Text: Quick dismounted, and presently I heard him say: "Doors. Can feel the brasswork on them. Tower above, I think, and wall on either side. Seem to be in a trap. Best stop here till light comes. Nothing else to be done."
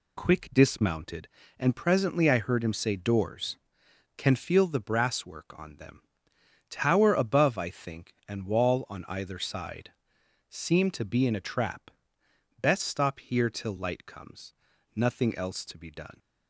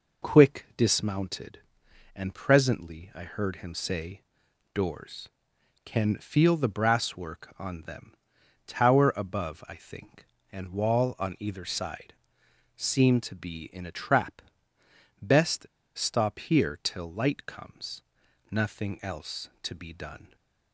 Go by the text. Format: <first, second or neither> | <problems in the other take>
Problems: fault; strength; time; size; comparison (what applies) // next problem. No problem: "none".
first | pauses between "Best" and "stop"; slight; at 15.6 s; 0.29 s long